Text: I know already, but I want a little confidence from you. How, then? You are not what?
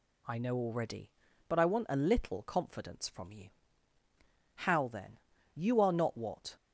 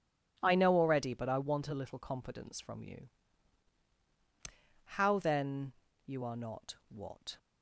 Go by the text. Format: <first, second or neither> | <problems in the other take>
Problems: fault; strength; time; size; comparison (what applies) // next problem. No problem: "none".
neither | none